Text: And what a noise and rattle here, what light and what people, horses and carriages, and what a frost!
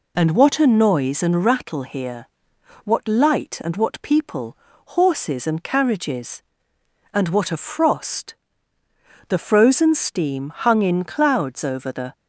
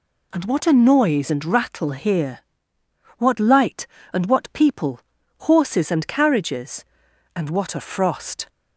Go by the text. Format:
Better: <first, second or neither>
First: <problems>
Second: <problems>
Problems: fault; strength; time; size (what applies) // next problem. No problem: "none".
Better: second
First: goes on to say "The frozen steam hung in clouds over the"; strong; from 9.2 s on; 2.8 s long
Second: none